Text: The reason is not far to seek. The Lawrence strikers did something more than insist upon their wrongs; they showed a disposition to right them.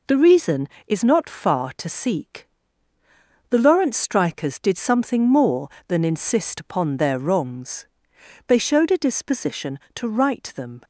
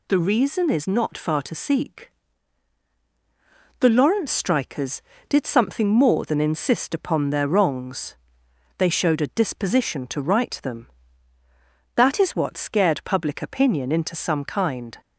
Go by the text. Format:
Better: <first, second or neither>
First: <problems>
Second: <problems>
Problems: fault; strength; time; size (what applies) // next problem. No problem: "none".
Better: first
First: none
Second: goes on to say "That is what scared public opinion into some kind"; strong; from 11.9 s on; 3.0 s long